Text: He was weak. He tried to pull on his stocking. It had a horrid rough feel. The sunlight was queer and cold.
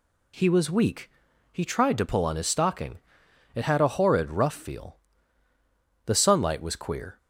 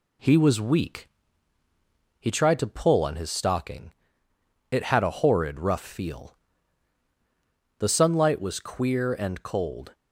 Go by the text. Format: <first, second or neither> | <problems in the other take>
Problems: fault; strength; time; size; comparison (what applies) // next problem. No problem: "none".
second | stops before "and cold"; at 7.1 s